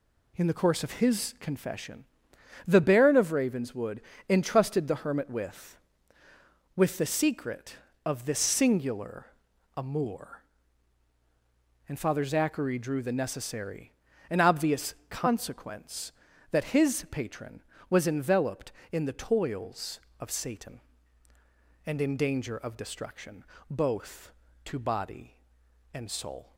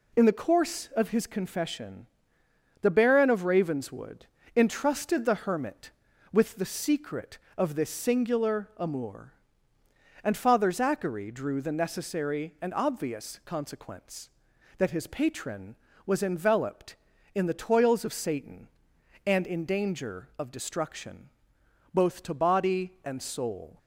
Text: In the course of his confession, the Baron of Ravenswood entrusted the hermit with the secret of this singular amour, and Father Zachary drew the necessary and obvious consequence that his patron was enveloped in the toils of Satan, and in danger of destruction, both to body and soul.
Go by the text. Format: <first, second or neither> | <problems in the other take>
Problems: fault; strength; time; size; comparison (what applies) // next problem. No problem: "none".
second | pauses between "Ravenswood" and "entrusted"; slight; at 4.0 s; 0.28 s long; slight in the second // says "with" twice; at 6.7 s // pauses between "singular" and "amour"; noticeable; at 9.2 s; 0.50 s long